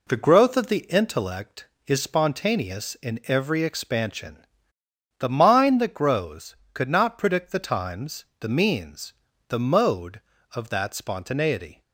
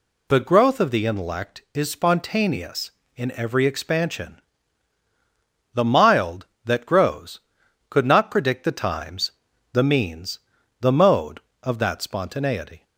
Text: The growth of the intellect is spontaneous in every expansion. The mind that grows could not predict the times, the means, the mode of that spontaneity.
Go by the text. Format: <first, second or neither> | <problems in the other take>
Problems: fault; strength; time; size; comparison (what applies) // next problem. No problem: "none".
first | says "mild" for "mind"; at 5.8 s